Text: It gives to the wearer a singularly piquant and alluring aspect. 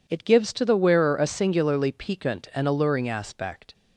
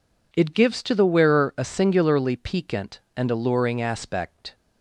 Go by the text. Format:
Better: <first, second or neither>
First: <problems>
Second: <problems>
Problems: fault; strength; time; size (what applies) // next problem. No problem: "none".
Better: neither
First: none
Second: none